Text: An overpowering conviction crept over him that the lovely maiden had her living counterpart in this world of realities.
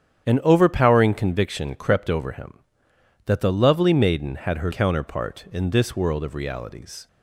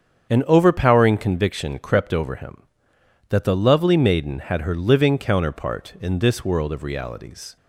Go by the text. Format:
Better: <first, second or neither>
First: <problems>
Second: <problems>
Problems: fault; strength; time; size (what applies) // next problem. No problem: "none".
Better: second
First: starts louder than the rest; strong; until 1.3 s; 9 dB // skips "living"; at 4.7 s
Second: starts louder than the rest; strong; until 1.3 s; 7.5 dB